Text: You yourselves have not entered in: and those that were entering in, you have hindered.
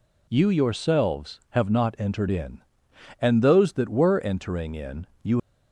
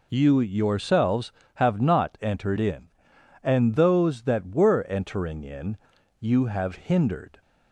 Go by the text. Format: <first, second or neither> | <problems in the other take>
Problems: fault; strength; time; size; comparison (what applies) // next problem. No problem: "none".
second | stops before "have hindered"; at 5.3 s